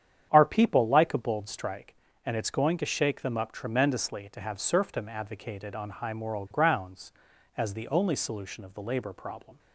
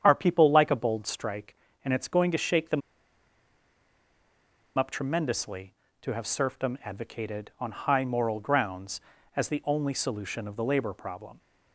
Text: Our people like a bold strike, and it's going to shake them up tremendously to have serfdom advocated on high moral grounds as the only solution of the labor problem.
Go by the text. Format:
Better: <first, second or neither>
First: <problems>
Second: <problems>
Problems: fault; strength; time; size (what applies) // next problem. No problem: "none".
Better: first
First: starts louder than the rest; strong; until 1.3 s; 9 dB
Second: starts louder than the rest; strong; until 1.0 s; 8.5 dB // pauses between "them" and "up"; strong; at 2.8 s; 1.9 s long